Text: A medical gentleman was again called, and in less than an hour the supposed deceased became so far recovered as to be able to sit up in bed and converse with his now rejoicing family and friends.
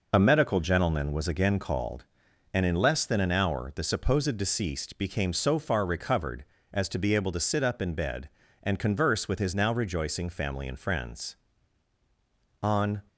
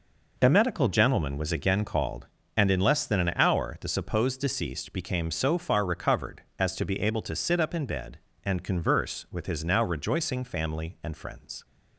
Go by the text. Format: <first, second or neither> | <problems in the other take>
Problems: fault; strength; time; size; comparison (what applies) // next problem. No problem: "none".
second | goes on to say "On"; slight; from 12.6 s on; 0.40 s long